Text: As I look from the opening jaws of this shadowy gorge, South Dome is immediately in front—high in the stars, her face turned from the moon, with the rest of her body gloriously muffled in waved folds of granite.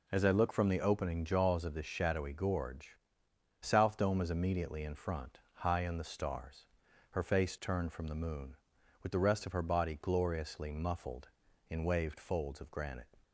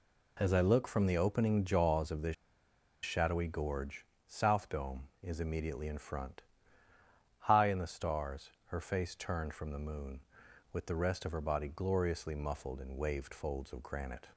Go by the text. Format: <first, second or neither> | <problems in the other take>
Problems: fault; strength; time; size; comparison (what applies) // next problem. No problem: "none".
first | pauses between "this" and "shadowy"; noticeable; at 2.3 s; 0.69 s long